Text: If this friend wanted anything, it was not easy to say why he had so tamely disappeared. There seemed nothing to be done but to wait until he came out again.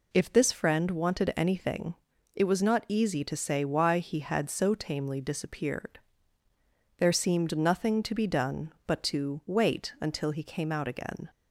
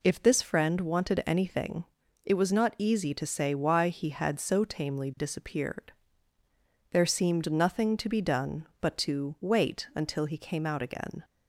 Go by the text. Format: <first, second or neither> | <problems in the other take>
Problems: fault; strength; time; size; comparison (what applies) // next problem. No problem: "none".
neither | none